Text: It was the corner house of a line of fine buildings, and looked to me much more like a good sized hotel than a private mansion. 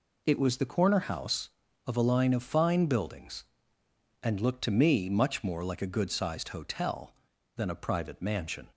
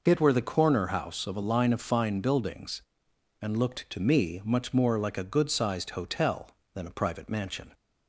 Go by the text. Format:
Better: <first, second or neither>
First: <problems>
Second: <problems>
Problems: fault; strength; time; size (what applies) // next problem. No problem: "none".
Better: first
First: none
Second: says "were" for "was"; at 0.2 s